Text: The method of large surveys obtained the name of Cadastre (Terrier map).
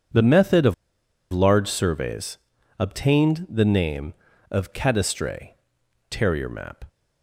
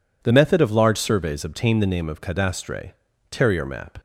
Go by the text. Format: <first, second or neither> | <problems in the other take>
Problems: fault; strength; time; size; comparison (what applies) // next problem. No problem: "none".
second | pauses between "of" and "large"; noticeable; at 0.7 s; 0.58 s long // pauses between "surveys" and "obtained"; at 2.3 s; 0.42 s long